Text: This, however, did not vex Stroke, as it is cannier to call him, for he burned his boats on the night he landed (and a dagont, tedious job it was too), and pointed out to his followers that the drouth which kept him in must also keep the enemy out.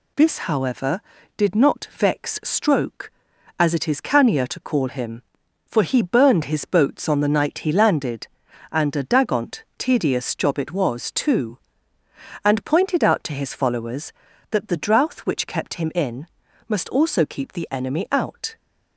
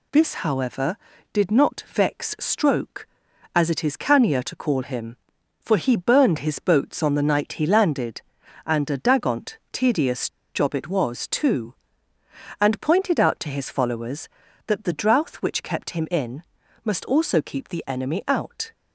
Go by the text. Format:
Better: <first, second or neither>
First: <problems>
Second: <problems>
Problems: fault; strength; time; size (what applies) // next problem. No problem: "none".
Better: first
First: pauses between "in" and "must"; at 16.2 s; 0.42 s long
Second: pauses between "tedious" and "job"; slight; at 10.2 s; 0.24 s long // pauses between "in" and "must"; at 16.4 s; 0.42 s long